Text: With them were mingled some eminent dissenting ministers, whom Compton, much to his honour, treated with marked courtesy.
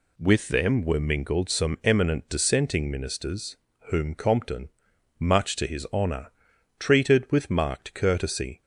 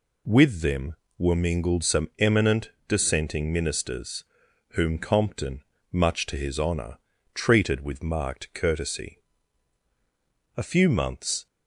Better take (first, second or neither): first